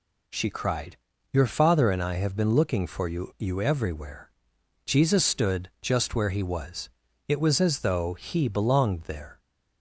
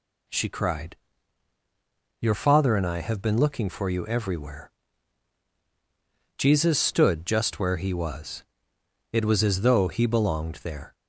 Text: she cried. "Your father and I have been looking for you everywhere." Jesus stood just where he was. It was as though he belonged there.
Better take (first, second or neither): second